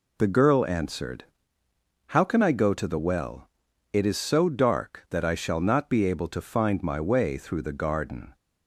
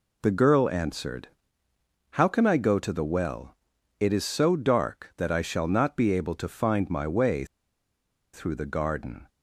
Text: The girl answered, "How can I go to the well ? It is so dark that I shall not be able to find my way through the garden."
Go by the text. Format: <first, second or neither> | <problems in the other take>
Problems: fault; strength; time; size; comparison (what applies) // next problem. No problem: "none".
first | pauses between "way" and "through"; noticeable; at 7.4 s; 0.89 s long